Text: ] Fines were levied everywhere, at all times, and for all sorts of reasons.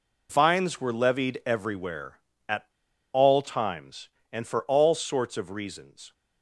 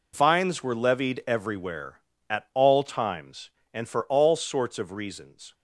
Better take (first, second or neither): second